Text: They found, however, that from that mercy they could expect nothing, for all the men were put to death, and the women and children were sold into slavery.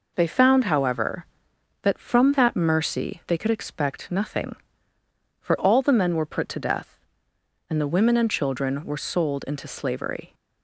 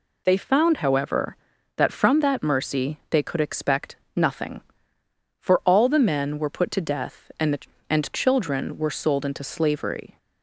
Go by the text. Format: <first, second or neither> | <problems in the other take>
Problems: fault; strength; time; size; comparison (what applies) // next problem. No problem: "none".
first | pauses between "expect" and "nothing"; slight; at 3.9 s; 0.20 s long // skips "women"; at 7.7 s